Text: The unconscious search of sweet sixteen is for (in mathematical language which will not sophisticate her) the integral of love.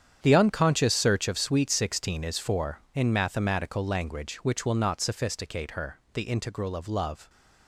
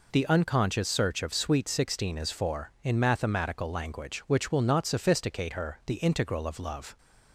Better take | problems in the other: second | gets quieter; strong; throughout; 13.5 dB

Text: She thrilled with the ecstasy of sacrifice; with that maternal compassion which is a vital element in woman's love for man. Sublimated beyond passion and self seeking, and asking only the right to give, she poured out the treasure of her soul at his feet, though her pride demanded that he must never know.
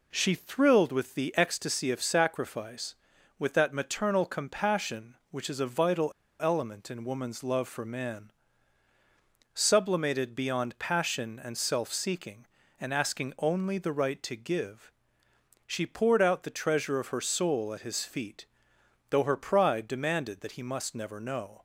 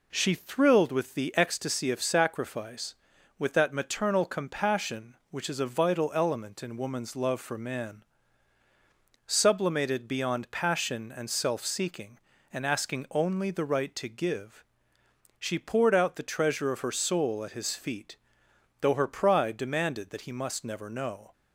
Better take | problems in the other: second | pauses between "vital" and "element"; slight; at 6.1 s; 0.29 s long

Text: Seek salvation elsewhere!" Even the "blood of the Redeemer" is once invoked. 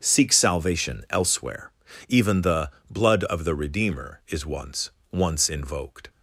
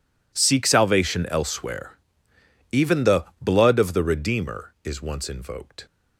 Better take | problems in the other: second | starts louder than the rest; strong; until 1.0 s; 7 dB // pauses between "the" and "blood"; slight; at 2.7 s; 0.18 s long; slight in the second // says "once" twice; at 5.1 s

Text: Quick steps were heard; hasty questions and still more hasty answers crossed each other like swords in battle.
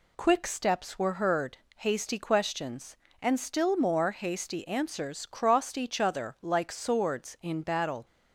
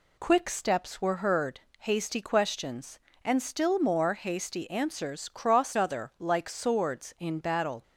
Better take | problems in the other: first | skips "each"; at 5.7 s

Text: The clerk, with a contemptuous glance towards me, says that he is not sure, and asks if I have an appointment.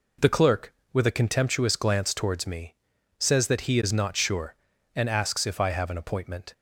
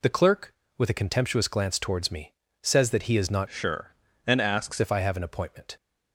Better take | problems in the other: first | changes voice from "sure" to "asks"; from 3.4 to 4.7 s; 1.3 s long

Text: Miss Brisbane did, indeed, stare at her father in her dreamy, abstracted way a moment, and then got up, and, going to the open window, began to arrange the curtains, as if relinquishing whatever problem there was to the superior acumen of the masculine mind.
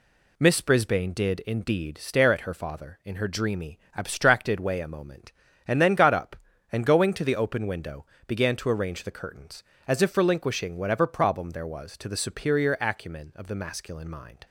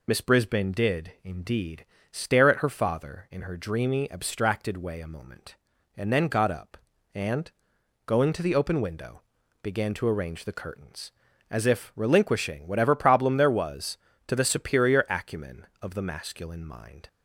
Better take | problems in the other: first | loses the start of "Miss"; at 0.0 s; 30 ms

